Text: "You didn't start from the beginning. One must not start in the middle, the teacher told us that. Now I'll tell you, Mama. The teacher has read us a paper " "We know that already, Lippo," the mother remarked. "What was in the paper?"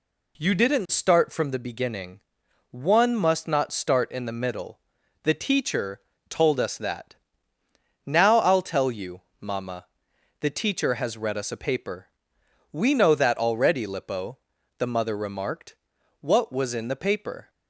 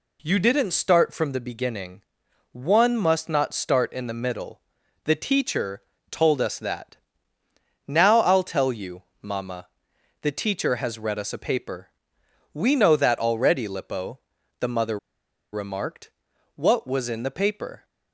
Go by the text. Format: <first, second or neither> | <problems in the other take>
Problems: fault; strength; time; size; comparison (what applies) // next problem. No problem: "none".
first | pauses between "teacher" and "told"; slight; at 5.8 s; 0.30 s long; slight in the first // pauses between "mother" and "remarked"; noticeable; at 14.9 s; 0.54 s long